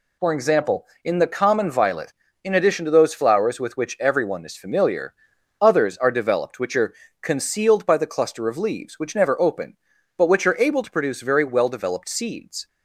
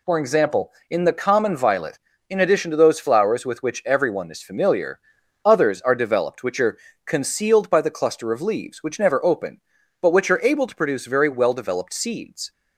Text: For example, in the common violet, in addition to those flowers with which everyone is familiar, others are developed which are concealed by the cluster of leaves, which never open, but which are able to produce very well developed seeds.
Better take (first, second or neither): neither